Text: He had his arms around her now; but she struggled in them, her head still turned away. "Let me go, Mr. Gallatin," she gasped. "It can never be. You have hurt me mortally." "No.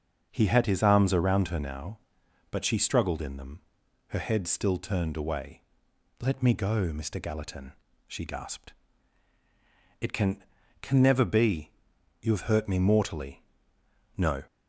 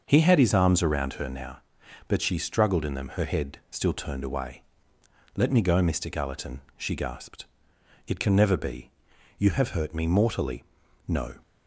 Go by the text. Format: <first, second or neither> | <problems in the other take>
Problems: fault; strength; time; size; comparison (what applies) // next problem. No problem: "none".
second | starts louder than the rest; until 1.3 s; 6.5 dB; also in the second // says "can" twice; at 10.8 s